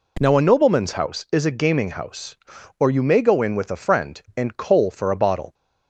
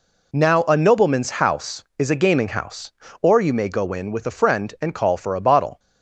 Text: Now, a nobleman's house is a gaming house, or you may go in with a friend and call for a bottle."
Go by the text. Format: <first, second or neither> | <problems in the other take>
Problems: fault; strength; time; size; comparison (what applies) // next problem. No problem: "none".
second | says "coal" for "call"; at 4.5 s